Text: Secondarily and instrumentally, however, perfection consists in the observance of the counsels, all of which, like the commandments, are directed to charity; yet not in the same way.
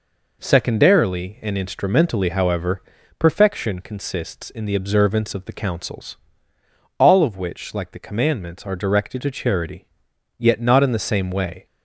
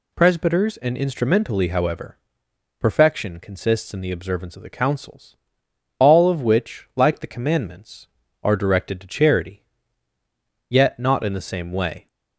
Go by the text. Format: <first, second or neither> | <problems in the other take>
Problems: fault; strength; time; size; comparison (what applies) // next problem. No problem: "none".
first | says "Presbyters" for "Secondarily"; at 0.1 s